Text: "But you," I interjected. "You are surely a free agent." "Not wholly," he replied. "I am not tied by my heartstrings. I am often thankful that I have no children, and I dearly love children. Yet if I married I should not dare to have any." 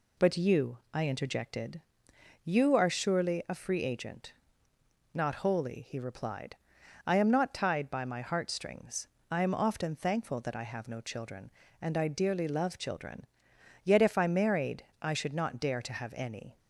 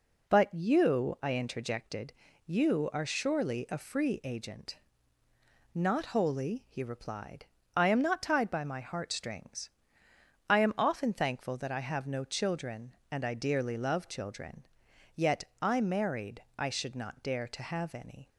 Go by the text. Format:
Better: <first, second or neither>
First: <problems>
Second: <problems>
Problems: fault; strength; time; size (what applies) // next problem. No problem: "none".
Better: first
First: pauses between "married" and "I"; slight; at 14.8 s; 0.16 s long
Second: skips "if"; at 15.5 s // pauses between "married" and "I"; slight; at 16.4 s; 0.16 s long